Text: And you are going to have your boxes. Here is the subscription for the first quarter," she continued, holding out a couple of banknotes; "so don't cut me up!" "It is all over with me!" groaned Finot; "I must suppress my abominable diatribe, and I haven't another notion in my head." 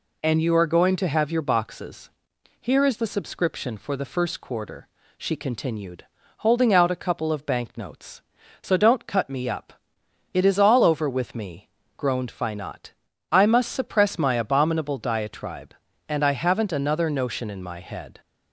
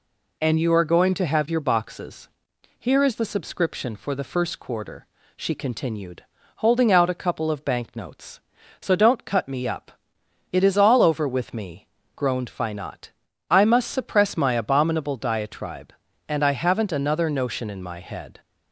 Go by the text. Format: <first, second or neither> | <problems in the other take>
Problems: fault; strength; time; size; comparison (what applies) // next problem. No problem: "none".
neither | none